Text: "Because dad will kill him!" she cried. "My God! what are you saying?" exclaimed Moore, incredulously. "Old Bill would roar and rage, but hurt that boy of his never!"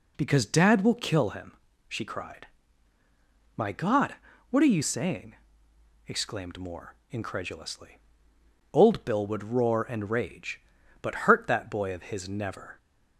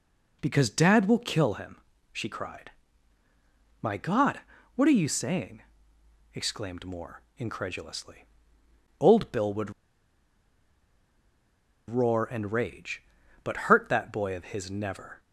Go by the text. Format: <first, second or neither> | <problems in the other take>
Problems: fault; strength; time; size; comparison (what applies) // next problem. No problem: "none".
first | pauses between "would" and "roar"; strong; at 9.7 s; 2.1 s long